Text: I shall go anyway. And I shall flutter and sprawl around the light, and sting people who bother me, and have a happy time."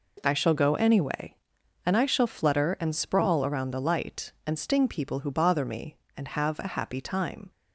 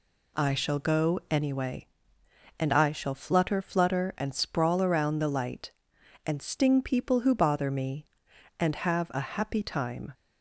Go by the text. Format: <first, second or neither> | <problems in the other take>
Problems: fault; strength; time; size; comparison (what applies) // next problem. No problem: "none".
first | says "flutter" twice; at 3.6 s